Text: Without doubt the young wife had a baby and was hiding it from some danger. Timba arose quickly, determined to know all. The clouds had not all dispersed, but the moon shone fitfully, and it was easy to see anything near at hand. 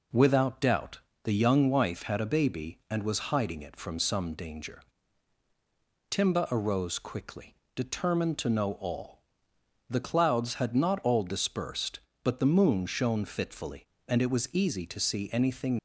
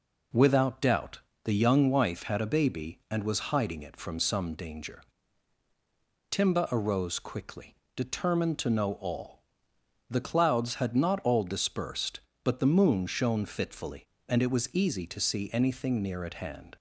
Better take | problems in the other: second | pauses between "doubt" and "the"; slight; at 0.9 s; 0.24 s long; slight in the second // stops before "near at hand"; at 15.7 s

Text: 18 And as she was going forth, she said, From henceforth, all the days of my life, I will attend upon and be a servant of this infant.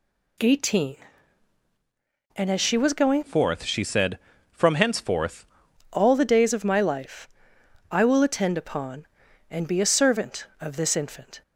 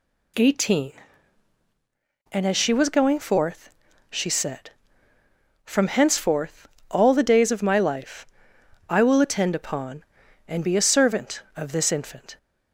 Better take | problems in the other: second | changes voice from "forth" to "henceforth"; from 3.2 to 5.4 s; 2.2 s long

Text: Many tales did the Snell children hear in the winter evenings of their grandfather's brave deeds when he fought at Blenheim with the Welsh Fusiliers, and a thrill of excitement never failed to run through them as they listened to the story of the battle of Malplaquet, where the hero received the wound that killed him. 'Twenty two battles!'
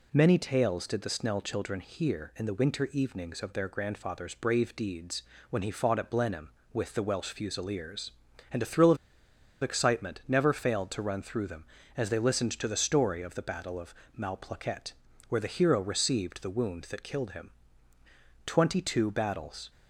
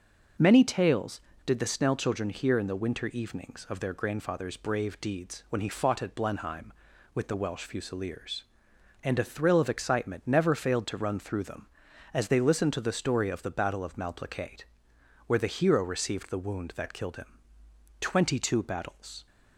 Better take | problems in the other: second | pauses between "deeds" and "when"; slight; at 5.2 s; 0.30 s long // pauses between "of" and "excitement"; noticeable; at 8.9 s; 0.65 s long // pauses between "of" and "Malplaquet"; slight; at 13.9 s; 0.24 s long

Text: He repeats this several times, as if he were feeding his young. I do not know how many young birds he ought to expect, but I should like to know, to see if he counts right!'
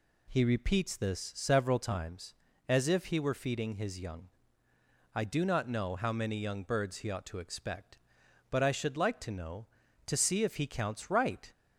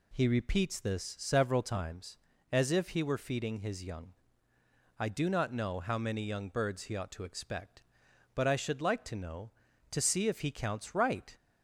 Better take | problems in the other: neither | none

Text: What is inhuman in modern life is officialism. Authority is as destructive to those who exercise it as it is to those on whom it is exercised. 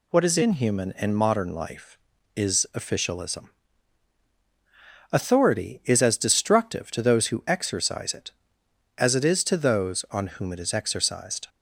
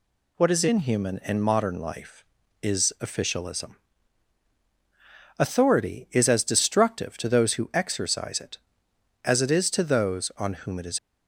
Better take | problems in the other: first | stops before "exercised"; at 10.9 s

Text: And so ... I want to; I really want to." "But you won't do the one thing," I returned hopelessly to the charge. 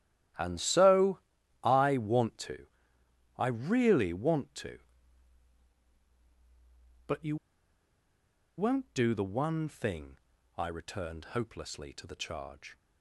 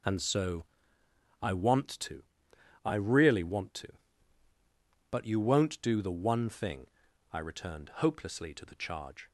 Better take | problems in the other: second | starts louder than the rest; strong; until 1.8 s; 12.5 dB // pauses between "you" and "won't"; at 7.3 s; 1.2 s long

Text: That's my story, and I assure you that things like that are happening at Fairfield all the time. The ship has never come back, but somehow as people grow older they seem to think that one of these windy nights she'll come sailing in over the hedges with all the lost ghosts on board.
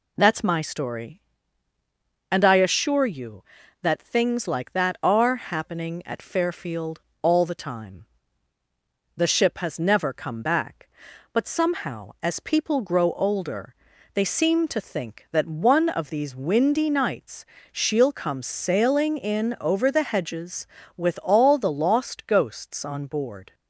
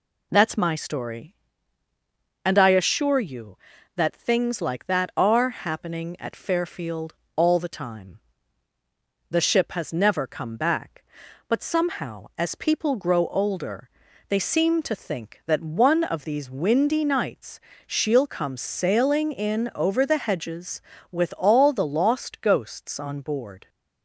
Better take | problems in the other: neither | pauses between "Fairfield" and "all"; slight; the same in both // pauses between "older" and "they"; the same in both // pauses between "nights" and "she'll"; slight; the same in both

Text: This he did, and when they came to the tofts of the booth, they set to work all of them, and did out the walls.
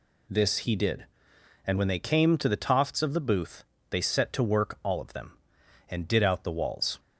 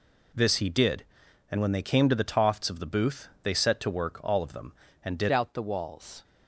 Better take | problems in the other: first | changes voice at "out"; from 5.2 s on; 1.0 s long

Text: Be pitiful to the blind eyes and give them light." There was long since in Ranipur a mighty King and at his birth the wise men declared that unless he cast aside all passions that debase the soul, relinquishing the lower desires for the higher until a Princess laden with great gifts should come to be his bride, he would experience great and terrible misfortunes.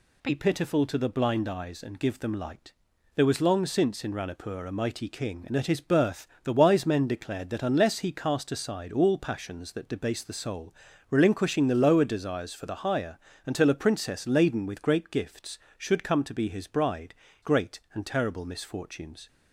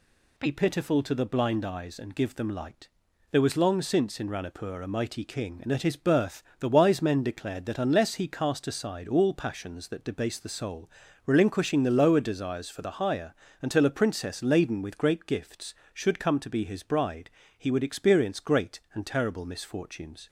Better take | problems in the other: second | pauses between "birth" and "the"; slight; at 6.2 s; 0.16 s long; slight in the second // pauses between "higher" and "until"; slight; at 13.1 s; 0.28 s long; slight in the second // skips "he would experience"; at 17.2 s

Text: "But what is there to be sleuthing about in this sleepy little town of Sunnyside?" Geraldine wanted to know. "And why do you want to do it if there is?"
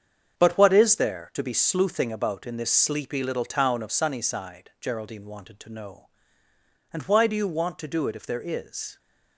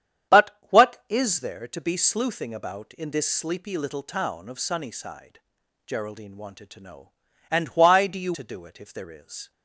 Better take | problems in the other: first | starts louder than the rest; strong; until 1.5 s; 9 dB; strong in the first // skips "want"; at 8.3 s

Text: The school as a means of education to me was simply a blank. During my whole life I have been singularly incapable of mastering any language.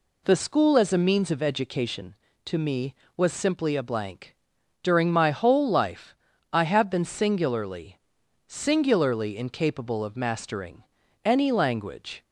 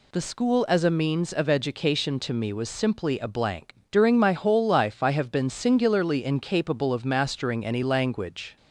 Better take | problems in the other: second | pauses between "life" and "I"; at 6.1 s; 0.38 s long // says "singularly" twice; at 8.4 s // pauses between "mastering" and "any"; at 10.8 s; 0.42 s long

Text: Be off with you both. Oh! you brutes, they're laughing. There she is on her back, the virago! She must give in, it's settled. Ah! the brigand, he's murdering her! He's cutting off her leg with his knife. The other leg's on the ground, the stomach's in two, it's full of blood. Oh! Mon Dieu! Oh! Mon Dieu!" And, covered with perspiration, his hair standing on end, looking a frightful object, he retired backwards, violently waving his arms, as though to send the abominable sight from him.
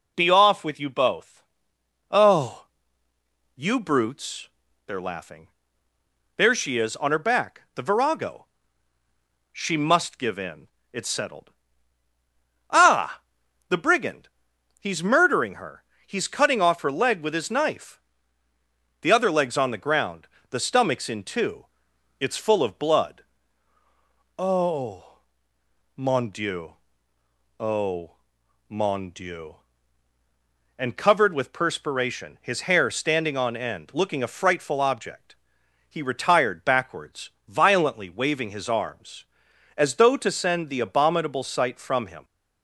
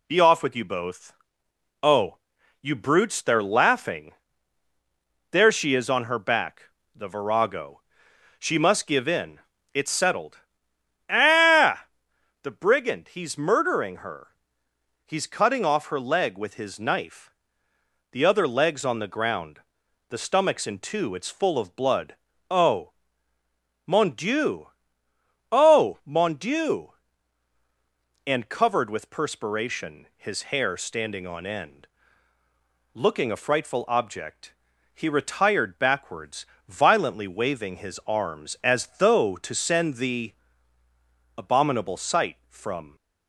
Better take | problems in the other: first | pauses between "the" and "abominable"; at 40.3 s; 1.0 s long // stops before "him"; at 42.9 s

